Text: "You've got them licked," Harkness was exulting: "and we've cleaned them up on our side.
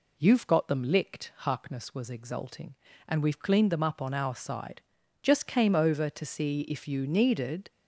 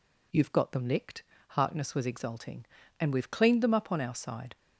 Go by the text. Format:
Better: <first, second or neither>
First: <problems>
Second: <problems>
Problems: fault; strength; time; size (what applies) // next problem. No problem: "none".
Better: second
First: goes on to say "Just came over to see if you needed"; strong; from 5.2 s on; 2.4 s long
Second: none